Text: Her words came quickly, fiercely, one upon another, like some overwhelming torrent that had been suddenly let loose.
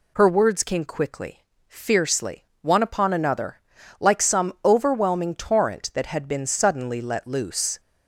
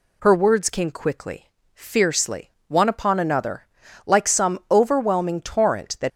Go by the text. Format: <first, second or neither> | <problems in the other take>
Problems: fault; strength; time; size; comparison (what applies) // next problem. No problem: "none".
first | stops before "had been suddenly let loose"; at 6.0 s